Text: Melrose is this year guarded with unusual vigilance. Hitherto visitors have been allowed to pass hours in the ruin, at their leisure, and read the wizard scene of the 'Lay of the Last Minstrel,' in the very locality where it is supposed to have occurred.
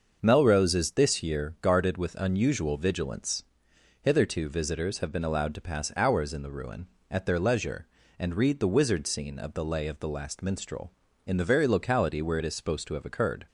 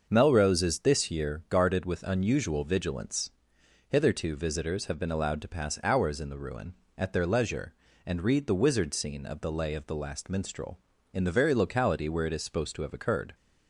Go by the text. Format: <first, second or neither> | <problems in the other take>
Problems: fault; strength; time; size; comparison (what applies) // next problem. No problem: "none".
neither | starts louder than the rest; the same in both